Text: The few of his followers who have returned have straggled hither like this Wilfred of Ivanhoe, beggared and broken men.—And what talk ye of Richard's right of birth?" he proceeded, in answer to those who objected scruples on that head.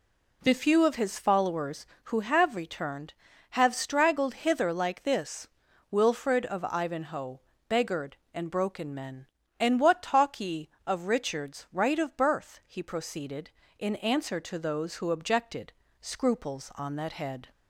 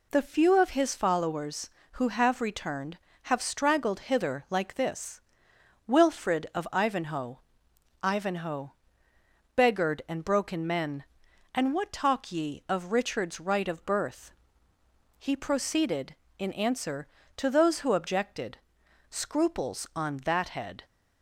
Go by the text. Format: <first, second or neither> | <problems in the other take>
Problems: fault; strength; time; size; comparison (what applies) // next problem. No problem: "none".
first | pauses between "this" and "Wilfred"; noticeable; at 5.2 s; 0.66 s long; also in the first // says "Ivanhoe" twice; at 8.0 s // pauses between "objected" and "scruples"; noticeable; at 18.5 s; 0.54 s long; slight in the first